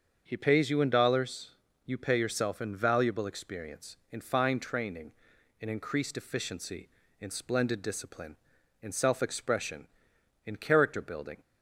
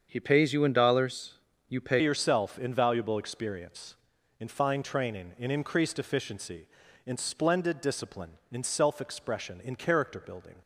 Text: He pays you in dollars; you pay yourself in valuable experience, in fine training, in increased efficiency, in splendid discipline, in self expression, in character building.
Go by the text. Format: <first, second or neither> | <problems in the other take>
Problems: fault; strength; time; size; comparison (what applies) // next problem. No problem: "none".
first | starts louder than the rest; until 1.1 s; 7 dB; also in the first // changes voice at "yourself"; from 2.0 s on; 8.5 s long